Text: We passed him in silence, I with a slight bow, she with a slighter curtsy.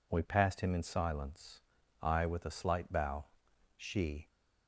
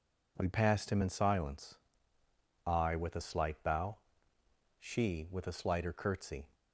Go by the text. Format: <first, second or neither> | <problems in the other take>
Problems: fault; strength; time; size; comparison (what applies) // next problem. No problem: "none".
second | stops before "with a slighter curtsy"; at 4.2 s